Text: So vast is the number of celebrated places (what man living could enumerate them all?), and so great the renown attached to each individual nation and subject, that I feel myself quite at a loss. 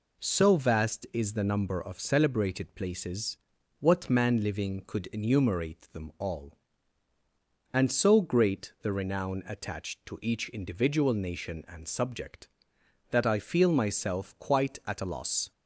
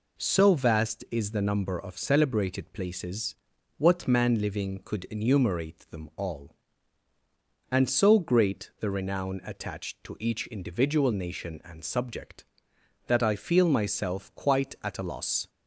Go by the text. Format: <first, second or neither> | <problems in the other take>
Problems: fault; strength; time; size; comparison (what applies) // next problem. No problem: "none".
neither | none